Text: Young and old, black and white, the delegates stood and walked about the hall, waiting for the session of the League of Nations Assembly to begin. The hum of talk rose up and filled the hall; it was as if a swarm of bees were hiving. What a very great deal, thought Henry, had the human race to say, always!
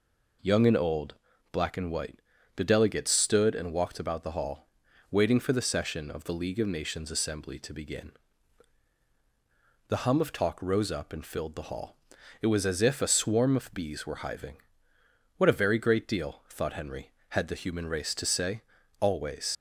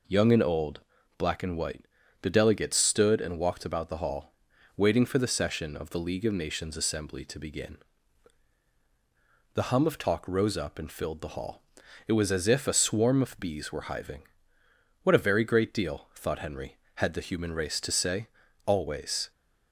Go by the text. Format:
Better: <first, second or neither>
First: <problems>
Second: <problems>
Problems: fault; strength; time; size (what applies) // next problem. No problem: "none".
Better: second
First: leaves "always" unfinished; at 19.5 s; 100 ms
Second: none